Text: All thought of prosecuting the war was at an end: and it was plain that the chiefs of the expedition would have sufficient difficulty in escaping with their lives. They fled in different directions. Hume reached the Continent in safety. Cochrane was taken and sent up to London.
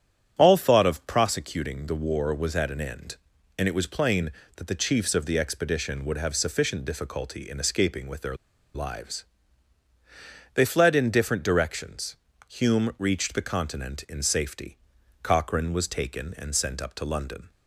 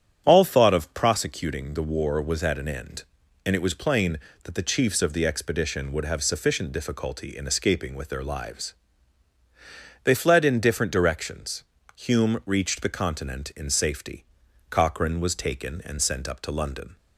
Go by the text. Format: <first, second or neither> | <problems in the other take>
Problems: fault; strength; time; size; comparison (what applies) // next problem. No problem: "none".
second | starts louder than the rest; strong; until 1.3 s; 9 dB; strong in the second // pauses between "their" and "lives"; at 8.3 s; 0.40 s long